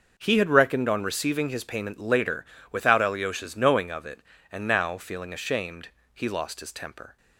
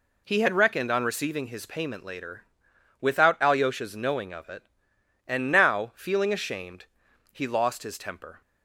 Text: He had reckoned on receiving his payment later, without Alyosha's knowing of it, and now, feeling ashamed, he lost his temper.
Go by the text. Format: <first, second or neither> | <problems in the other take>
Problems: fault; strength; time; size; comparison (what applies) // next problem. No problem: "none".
neither | none